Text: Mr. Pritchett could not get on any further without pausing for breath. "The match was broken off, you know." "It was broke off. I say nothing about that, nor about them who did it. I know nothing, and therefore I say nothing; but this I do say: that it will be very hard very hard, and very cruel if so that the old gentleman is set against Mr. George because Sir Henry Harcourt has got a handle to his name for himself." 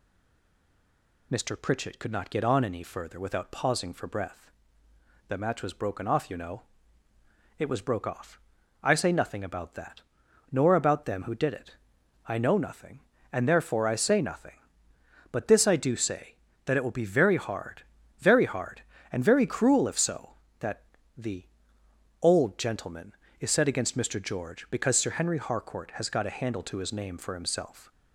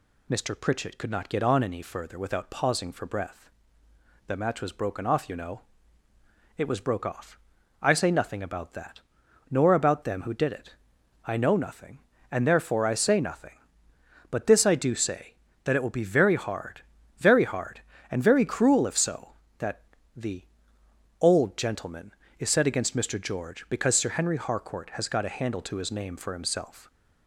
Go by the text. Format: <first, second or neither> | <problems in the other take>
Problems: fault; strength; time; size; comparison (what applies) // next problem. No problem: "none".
second | stays silent before the first word; noticeable; until 1.3 s; 1.3 s long // pauses between "hard" and "very"; slight; at 17.8 s; 0.36 s long; slight in the second // pauses between "that" and "the"; slight; at 20.8 s; 0.32 s long; slight in the second // pauses between "the" and "old"; noticeable; at 21.4 s; 0.76 s long; noticeable in the second